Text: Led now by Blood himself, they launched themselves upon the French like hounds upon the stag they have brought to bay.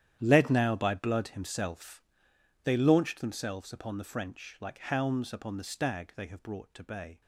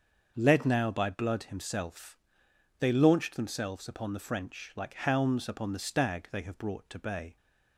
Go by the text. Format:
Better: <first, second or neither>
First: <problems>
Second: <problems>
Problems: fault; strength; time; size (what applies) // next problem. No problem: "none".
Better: second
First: gets quieter; strong; throughout; 15.5 dB // starts louder than the rest; strong; until 1.2 s; 10.5 dB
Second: starts louder than the rest; until 1.3 s; 6.5 dB